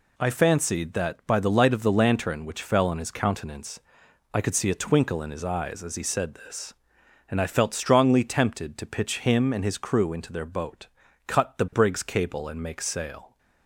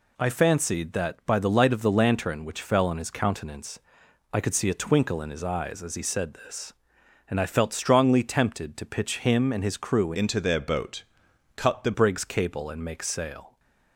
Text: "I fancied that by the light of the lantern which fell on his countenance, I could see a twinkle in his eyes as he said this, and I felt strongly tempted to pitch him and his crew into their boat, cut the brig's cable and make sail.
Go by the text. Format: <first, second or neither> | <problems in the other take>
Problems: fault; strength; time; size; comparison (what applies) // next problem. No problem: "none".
first | changes voice from "into" to "the"; from 10.1 to 11.9 s; 1.8 s long